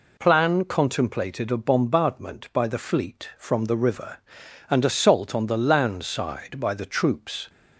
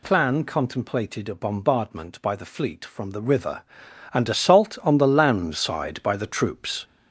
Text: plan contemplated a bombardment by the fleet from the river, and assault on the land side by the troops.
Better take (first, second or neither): first